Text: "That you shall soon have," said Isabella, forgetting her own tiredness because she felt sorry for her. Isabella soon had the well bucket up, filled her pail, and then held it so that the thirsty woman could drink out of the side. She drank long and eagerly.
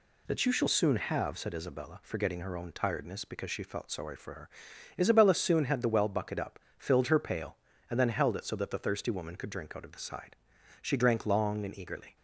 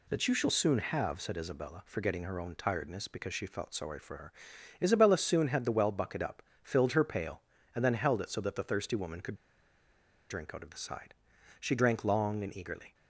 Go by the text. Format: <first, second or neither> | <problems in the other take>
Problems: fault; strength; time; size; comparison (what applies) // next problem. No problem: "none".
first | pauses between "could" and "drink"; noticeable; at 9.3 s; 0.95 s long